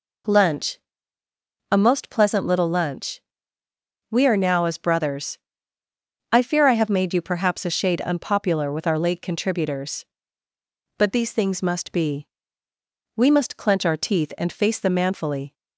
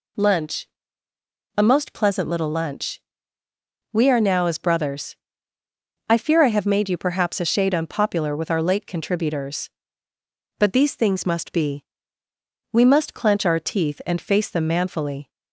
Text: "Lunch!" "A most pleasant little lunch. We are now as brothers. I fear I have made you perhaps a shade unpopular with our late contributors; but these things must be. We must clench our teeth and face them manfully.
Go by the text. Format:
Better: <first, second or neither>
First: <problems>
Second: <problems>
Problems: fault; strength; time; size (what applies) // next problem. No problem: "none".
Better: neither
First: none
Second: none